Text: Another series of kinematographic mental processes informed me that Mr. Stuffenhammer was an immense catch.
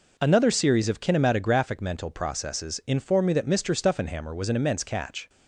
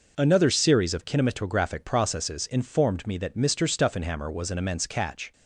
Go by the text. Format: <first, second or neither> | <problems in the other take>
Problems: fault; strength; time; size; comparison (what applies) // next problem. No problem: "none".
first | skips "mental"; at 1.8 s